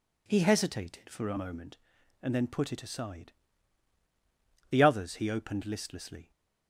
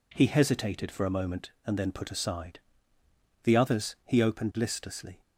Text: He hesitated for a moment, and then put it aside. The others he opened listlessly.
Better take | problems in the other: first | skips "it"; at 2.1 s

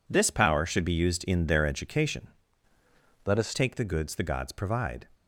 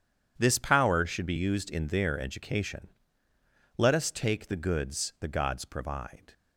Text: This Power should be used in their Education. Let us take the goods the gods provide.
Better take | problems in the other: second | changes voice from "Let" to "us"; from 3.2 to 3.5 s; 0.3 s long

